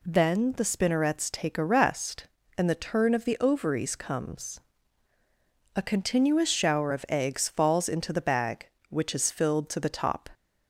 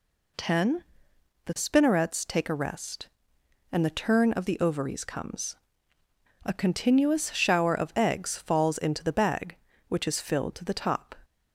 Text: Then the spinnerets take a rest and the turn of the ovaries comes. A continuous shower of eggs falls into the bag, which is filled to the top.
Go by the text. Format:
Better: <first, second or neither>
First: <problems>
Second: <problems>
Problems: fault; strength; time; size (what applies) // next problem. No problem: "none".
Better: first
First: none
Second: says "Ten" for "Then"; at 0.3 s